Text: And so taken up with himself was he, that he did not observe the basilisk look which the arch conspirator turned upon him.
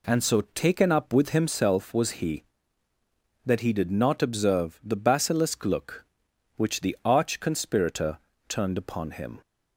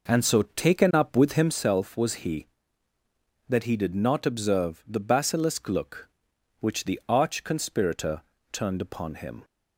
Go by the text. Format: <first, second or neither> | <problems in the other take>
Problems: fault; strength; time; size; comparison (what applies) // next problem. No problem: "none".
first | starts louder than the rest; noticeable; until 1.7 s; 5.5 dB // pauses between "conspirator" and "turned"; slight; at 8.2 s; 0.30 s long; slight in the first